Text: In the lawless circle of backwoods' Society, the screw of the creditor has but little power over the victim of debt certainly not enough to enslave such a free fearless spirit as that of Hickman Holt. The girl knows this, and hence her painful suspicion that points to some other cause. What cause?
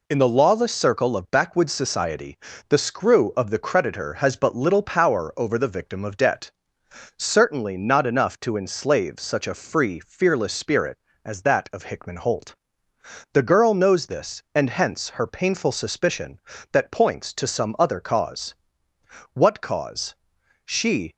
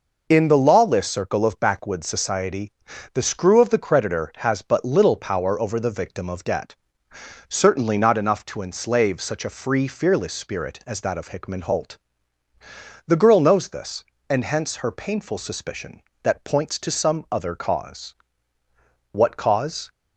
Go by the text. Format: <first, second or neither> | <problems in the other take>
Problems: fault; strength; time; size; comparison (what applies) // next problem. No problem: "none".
second | pauses between "debt" and "certainly"; noticeable; at 6.5 s; 0.66 s long; noticeable in the second // goes on to say "She"; from 20.6 s on; 0.50 s long